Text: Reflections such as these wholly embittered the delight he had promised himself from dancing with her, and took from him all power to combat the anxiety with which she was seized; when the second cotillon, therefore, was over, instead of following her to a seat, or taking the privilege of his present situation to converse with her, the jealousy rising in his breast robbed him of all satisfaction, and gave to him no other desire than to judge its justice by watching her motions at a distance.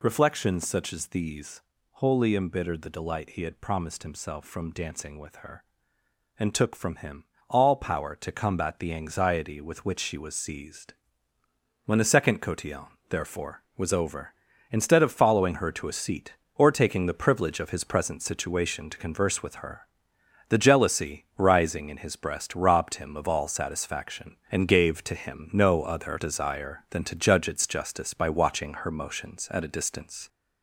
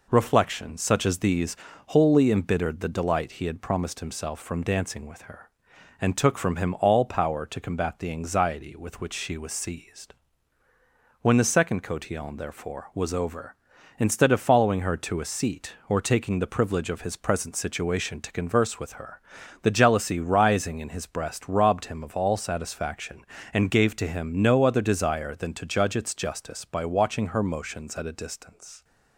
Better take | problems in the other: second | gets louder; noticeable; throughout; 4 dB // pauses between "these" and "wholly"; slight; at 1.6 s; 0.30 s long; slight in the second // pauses between "him" and "all"; slight; at 7.2 s; 0.24 s long

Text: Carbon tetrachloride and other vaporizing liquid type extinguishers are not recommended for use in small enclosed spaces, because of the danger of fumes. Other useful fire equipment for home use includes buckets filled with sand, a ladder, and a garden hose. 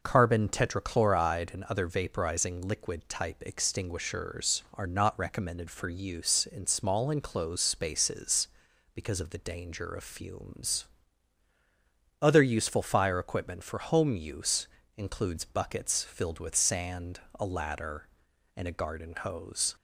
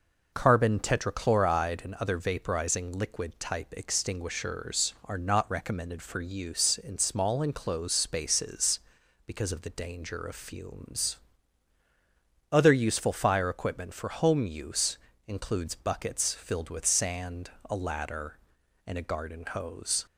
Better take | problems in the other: neither | pauses between "use" and "includes"; slight; the same in both

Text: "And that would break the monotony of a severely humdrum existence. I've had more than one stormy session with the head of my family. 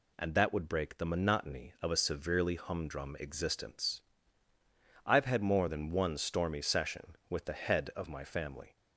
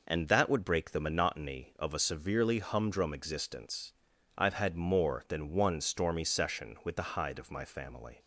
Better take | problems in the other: first | says "hide" for "head"; at 7.1 s

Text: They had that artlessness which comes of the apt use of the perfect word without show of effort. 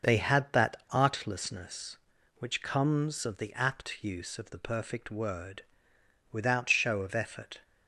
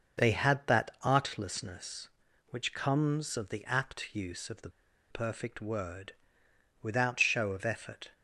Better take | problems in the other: first | starts louder than the rest; until 1.3 s; 6 dB; also in the first // pauses between "the" and "perfect"; at 4.6 s; 0.41 s long // pauses between "word" and "without"; noticeable; at 6.1 s; 0.68 s long; noticeable in the first

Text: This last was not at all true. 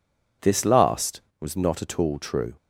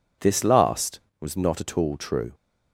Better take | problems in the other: neither | none

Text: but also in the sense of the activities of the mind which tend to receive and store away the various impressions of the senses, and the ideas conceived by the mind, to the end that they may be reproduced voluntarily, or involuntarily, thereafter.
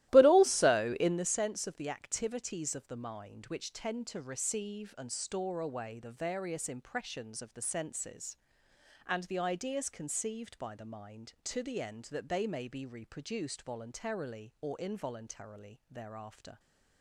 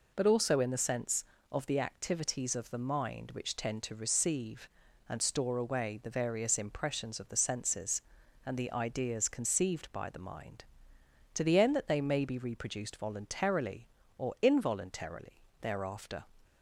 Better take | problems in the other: second | starts louder than the rest; strong; until 1.3 s; 15.5 dB

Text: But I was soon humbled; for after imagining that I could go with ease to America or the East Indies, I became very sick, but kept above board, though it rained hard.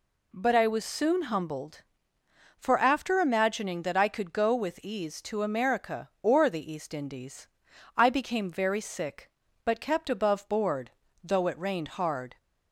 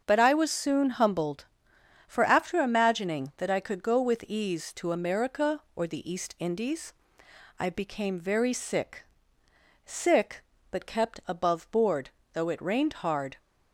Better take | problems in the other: first | starts louder than the rest; until 1.0 s; 7 dB // says "sick" twice; at 9.8 s

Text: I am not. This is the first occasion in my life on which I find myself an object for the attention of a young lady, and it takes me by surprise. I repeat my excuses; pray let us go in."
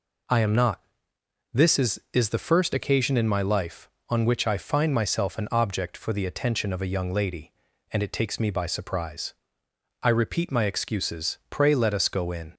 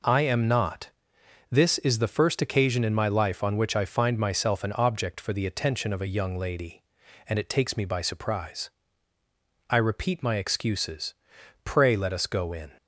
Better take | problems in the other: second | says "is" twice; at 2.1 s

